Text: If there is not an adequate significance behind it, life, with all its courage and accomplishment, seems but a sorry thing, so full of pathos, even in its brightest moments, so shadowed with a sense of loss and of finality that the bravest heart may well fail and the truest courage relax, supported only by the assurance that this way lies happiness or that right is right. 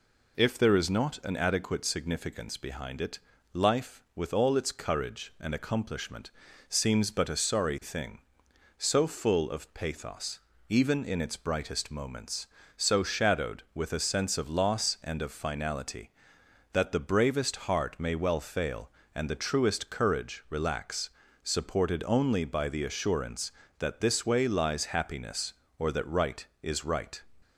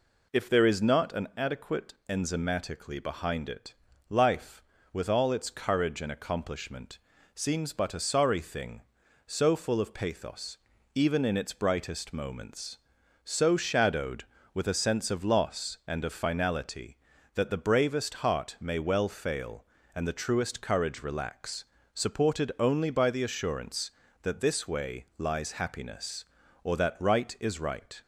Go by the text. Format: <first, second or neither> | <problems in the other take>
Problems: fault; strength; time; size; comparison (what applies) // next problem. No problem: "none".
first | says "enzymatically" for "significance"; at 2.0 s